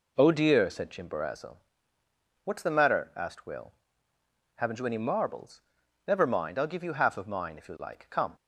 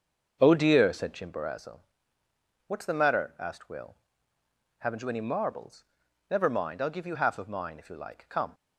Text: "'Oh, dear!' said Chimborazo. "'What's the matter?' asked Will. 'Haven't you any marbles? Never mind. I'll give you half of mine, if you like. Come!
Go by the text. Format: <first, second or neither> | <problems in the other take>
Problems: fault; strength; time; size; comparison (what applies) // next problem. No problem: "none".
first | starts louder than the rest; until 1.4 s; 6.5 dB